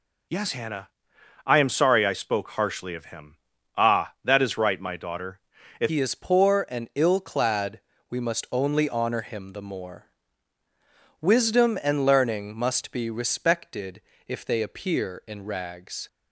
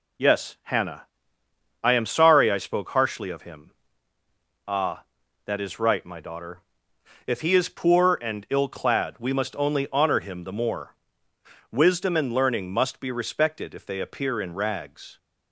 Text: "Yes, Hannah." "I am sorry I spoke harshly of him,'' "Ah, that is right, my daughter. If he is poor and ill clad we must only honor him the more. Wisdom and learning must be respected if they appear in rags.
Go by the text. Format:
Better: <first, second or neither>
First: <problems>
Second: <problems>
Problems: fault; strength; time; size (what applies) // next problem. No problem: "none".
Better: second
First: changes voice at "he"; from 5.9 s on; 10.1 s long // pauses between "clad" and "we"; slight; at 7.8 s; 0.28 s long // pauses between "respected" and "if"; slight; at 14.0 s; 0.28 s long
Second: none